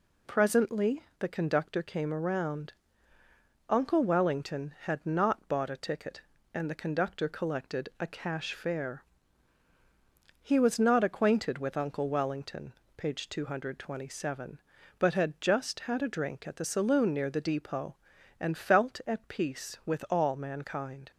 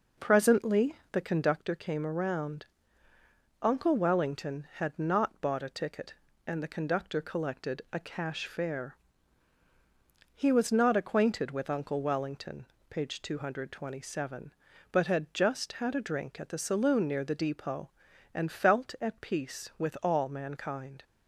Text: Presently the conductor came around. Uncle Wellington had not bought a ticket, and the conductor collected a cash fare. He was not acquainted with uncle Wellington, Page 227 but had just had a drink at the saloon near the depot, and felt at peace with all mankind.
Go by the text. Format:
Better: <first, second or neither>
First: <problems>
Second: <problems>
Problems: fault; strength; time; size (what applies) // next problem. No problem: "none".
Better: first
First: pauses between "Presently" and "the"; slight; at 1.0 s; 0.16 s long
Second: starts louder than the rest; noticeable; until 1.6 s; 5 dB // pauses between "Presently" and "the"; slight; at 0.9 s; 0.16 s long